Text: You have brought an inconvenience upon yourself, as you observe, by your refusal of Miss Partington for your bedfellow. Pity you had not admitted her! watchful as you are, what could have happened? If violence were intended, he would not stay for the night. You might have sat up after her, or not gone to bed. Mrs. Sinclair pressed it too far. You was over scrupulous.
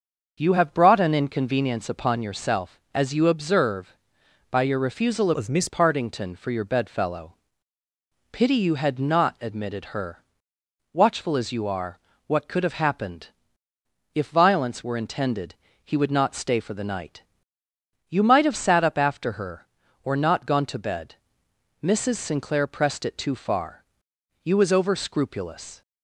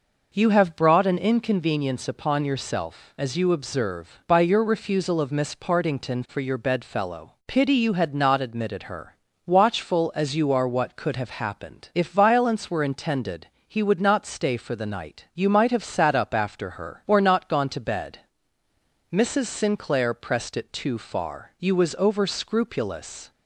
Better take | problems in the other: second | starts louder than the rest; until 1.4 s; 6.5 dB // changes voice from "of" to "Miss"; from 5.3 to 5.6 s; 0.3 s long

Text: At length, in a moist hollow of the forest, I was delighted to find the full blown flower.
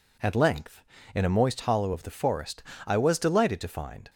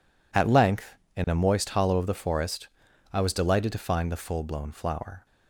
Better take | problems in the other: second | stops before "the full blown flower"; at 4.0 s

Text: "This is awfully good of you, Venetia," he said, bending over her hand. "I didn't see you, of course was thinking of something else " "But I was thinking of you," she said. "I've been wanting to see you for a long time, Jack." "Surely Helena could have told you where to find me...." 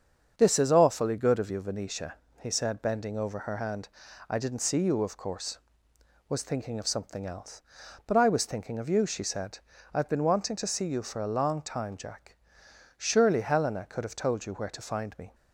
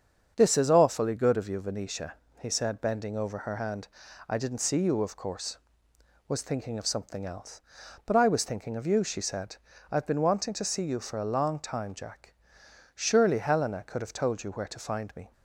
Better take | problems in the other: neither | starts louder than the rest; strong; the same in both

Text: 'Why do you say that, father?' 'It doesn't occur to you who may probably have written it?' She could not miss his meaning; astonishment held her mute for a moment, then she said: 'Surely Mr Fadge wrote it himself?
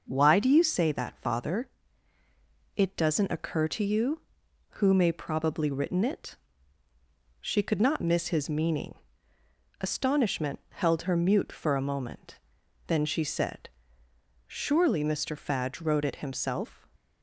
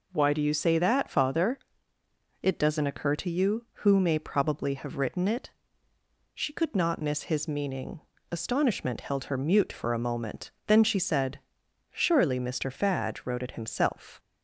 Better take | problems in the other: second | skips "have"; at 5.6 s

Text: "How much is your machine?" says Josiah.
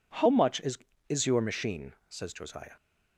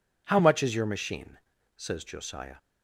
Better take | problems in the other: second | says "is" twice; at 1.0 s

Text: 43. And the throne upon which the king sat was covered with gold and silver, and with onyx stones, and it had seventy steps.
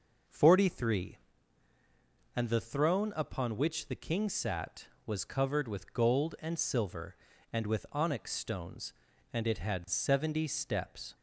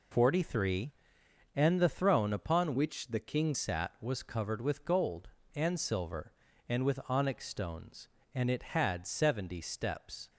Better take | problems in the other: first | changes voice from "which" to "king"; from 2.7 to 3.5 s; 0.8 s long

